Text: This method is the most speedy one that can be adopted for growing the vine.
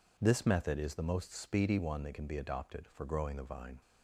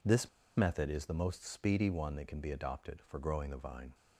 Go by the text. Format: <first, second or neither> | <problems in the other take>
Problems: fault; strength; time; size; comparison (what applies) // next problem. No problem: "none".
first | pauses between "This" and "method"; slight; at 0.2 s; 0.29 s long